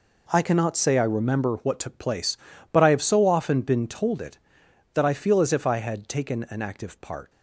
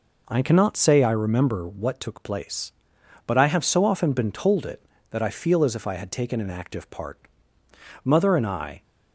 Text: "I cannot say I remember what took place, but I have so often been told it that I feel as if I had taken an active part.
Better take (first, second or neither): first